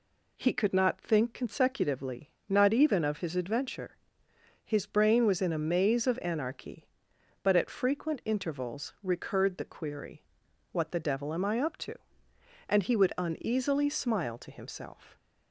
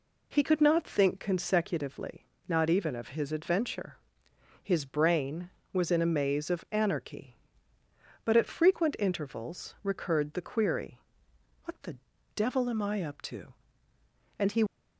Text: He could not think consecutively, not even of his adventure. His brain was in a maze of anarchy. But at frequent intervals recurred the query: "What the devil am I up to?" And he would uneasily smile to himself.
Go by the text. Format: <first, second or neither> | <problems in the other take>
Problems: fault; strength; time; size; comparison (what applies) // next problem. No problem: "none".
first | pauses between "the" and "devil"; slight; at 11.9 s; 0.36 s long // stops before "would uneasily smile to himself"; at 14.6 s